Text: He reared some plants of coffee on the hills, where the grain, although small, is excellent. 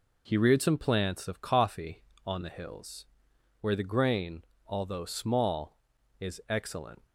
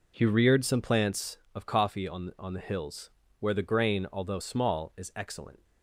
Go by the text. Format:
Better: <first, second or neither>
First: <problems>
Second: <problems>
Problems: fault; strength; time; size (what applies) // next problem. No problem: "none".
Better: first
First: none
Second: says "on" twice; at 2.3 s